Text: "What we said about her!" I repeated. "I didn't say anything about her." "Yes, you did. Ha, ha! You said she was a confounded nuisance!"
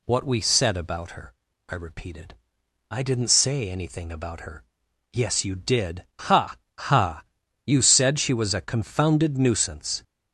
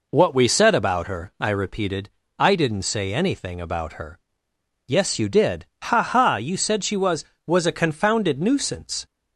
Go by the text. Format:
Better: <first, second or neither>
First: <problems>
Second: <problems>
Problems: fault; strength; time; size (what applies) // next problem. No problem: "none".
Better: first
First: none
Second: says "was" twice; at 7.4 s